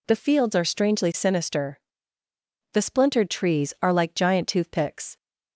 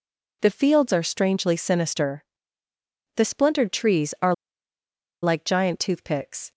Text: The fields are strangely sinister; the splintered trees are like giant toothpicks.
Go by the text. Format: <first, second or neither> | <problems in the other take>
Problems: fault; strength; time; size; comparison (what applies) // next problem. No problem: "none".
first | pauses between "are" and "like"; noticeable; at 4.3 s; 0.88 s long